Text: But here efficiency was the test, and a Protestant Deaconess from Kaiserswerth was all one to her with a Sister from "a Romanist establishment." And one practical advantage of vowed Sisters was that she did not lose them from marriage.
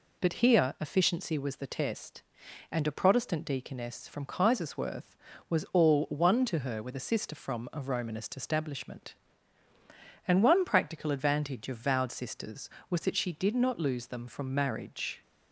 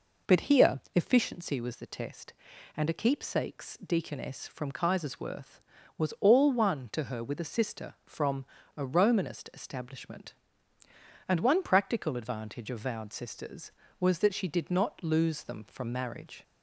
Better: first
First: none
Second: pauses between "here" and "efficiency"; slight; at 0.7 s; 0.16 s long // says "Keepsakes" for "Protestant"; at 2.9 s // pauses between "from" and "a"; slight; at 8.4 s; 0.32 s long

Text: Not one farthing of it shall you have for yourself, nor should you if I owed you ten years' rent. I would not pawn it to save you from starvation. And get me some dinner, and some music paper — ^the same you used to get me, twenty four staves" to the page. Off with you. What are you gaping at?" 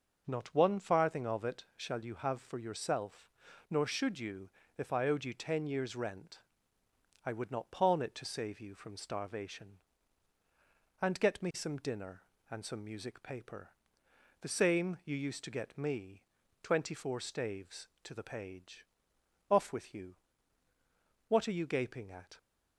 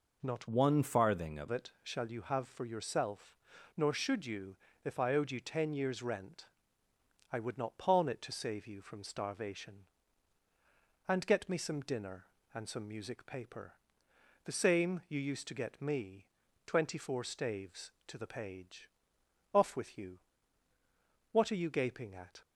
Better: first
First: pauses between "you" and "if"; slight; at 4.4 s; 0.28 s long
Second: changes voice from "one" to "of"; from 0.4 to 1.4 s; 1.0 s long // pauses between "you" and "if"; slight; at 4.5 s; 0.28 s long

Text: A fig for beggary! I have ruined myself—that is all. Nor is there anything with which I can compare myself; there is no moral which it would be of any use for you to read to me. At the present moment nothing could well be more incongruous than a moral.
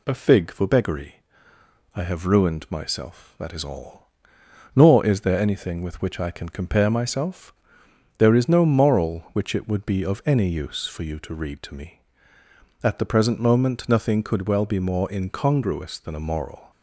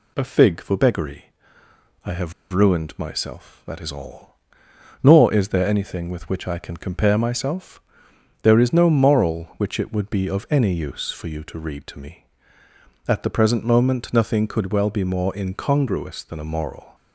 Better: first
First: none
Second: pauses between "have" and "ruined"; slight; at 2.3 s; 0.20 s long

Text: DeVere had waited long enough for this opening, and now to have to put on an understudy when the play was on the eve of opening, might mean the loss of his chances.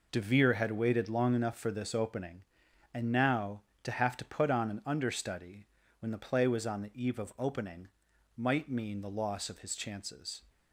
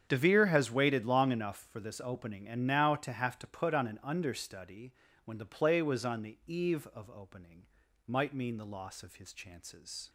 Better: first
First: pauses between "understudy" and "when"; slight; at 5.6 s; 0.32 s long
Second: starts louder than the rest; strong; until 1.1 s; 8 dB // says "has" for "had"; at 0.4 s // pauses between "understudy" and "when"; slight; at 4.9 s; 0.32 s long

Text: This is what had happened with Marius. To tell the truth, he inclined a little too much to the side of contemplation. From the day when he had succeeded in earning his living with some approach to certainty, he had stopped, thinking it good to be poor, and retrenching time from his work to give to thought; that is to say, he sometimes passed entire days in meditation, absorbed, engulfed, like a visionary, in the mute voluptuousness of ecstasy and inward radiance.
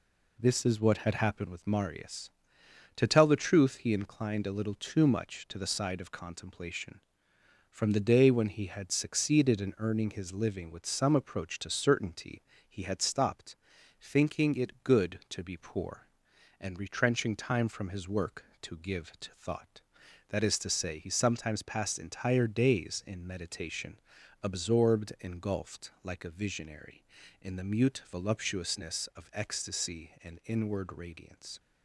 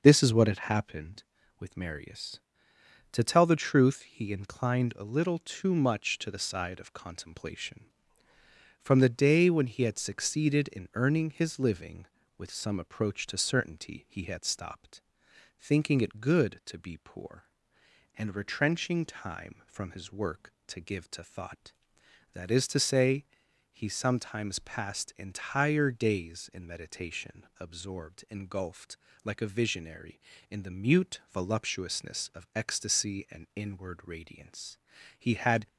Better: first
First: none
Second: goes on to say "He had"; slight; from 35.1 s on; 0.48 s long

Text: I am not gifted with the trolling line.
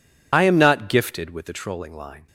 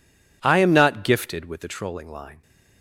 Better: second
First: loses the start of "I"; at 0.3 s; 60 ms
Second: none

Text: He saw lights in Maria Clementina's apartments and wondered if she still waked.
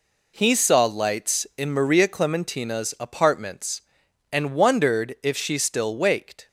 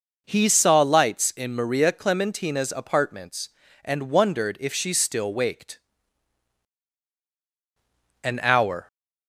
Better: first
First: none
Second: goes on to say "An hour"; noticeable; from 8.2 s on; 0.64 s long

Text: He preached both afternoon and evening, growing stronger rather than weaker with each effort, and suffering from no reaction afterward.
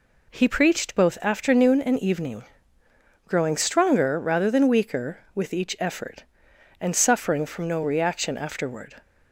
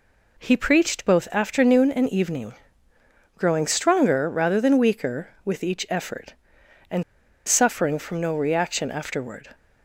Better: first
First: none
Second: pauses between "and" and "suffering"; at 7.0 s; 0.43 s long

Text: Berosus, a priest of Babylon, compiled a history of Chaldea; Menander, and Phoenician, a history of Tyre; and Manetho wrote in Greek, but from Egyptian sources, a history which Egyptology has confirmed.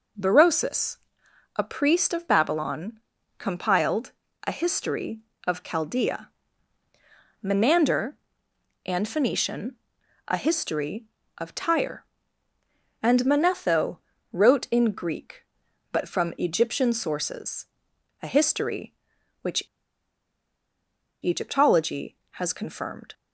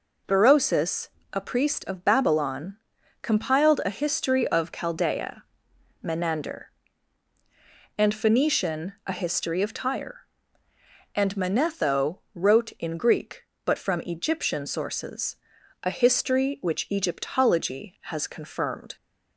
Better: second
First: pauses between "compiled" and "a"; slight; at 4.1 s; 0.34 s long // pauses between "Manetho" and "wrote"; slight; at 13.9 s; 0.32 s long // pauses between "which" and "Egyptology"; strong; at 19.6 s; 1.5 s long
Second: none

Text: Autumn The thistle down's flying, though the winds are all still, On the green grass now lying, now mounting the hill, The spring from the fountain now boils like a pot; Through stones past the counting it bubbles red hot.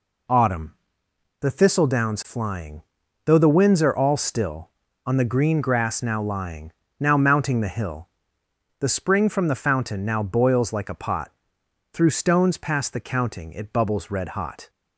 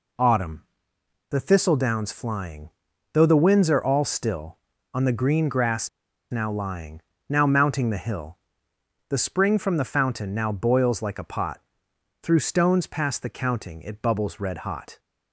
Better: first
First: pauses between "Autumn" and "The"; noticeable; at 0.7 s; 0.70 s long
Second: pauses between "Autumn" and "The"; noticeable; at 0.6 s; 0.70 s long // pauses between "grass" and "now"; at 5.8 s; 0.41 s long

